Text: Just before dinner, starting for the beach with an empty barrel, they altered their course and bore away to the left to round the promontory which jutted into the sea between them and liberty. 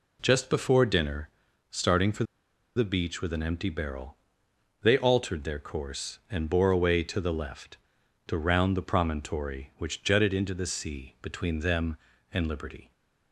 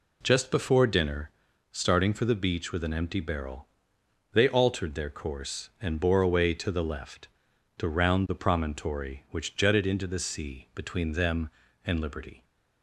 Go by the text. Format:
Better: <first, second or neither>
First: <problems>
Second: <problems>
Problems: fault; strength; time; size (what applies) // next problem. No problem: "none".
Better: second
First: pauses between "for" and "the"; noticeable; at 2.2 s; 0.51 s long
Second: none